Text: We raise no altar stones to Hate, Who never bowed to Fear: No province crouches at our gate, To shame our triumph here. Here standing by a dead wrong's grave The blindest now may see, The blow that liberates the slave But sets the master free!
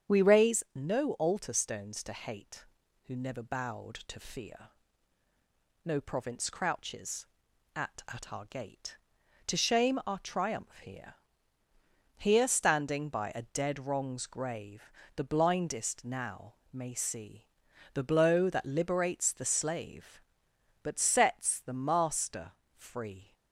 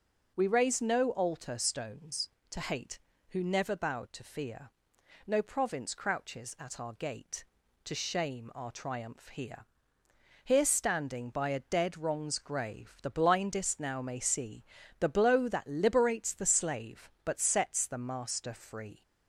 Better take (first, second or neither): second